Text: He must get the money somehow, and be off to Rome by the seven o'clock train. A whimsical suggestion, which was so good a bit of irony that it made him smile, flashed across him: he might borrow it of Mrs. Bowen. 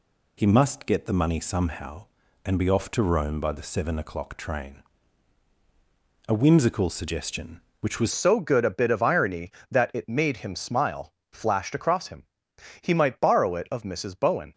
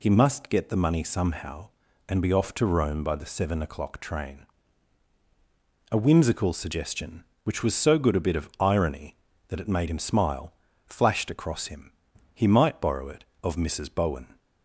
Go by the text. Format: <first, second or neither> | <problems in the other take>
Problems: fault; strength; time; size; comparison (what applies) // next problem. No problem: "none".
second | changes voice at "so"; from 8.1 s on; 6.4 s long